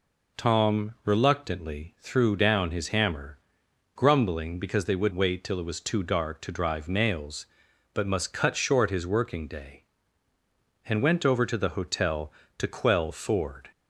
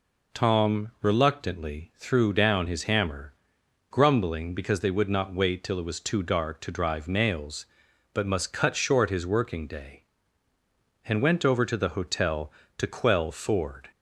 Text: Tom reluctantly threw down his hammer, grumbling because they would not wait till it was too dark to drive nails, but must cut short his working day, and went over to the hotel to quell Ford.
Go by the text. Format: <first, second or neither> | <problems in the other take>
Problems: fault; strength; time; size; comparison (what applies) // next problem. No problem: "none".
second | skips "not"; at 5.1 s